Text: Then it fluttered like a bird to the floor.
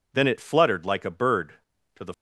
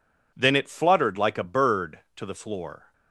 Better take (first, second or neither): second